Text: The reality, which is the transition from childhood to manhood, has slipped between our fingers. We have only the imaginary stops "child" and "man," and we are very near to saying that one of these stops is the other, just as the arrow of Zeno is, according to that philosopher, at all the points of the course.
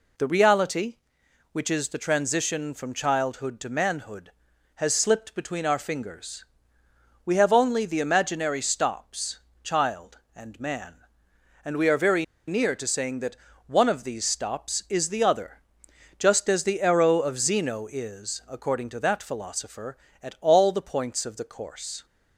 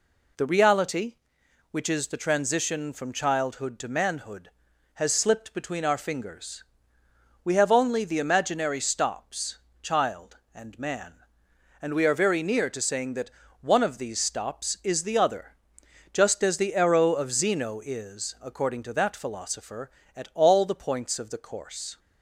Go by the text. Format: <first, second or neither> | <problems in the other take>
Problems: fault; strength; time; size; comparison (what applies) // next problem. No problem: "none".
second | pauses between "stops" and "child"; slight; at 9.4 s; 0.22 s long; slight in the second // pauses between "very" and "near"; slight; at 12.2 s; 0.23 s long // pauses between "that" and "one"; slight; at 13.3 s; 0.32 s long; slight in the second